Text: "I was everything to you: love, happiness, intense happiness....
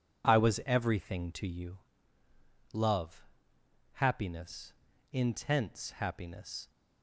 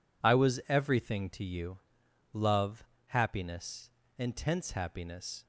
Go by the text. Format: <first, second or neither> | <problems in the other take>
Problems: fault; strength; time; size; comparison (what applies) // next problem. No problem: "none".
neither | none